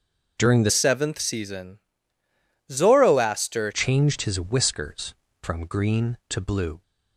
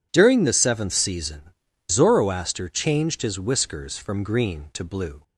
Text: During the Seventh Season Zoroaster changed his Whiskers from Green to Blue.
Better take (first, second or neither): second